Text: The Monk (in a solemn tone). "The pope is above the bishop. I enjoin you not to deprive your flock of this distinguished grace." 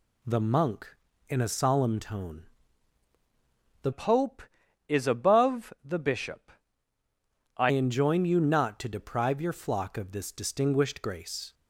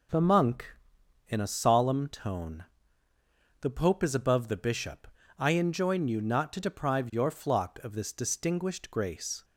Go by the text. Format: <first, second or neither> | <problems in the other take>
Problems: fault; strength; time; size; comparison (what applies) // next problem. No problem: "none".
second | changes voice from "pope" to "I"; from 3.9 to 7.7 s; 3.8 s long